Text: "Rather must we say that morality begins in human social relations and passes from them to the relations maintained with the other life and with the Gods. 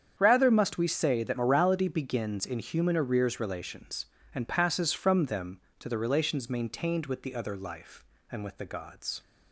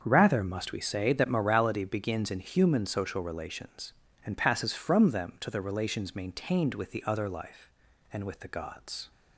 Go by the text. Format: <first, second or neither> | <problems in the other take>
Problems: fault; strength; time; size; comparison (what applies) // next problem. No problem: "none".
second | starts louder than the rest; strong; until 1.1 s; 8 dB; also in the second // says "arrears" for "social"; at 2.9 s